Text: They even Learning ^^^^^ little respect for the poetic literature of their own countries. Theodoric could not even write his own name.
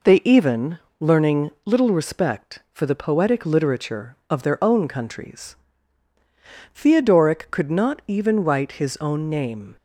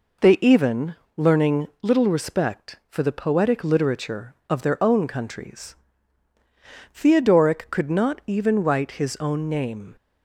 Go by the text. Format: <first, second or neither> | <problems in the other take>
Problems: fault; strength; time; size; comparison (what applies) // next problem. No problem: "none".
neither | pauses between "even" and "Learning"; slight; the same in both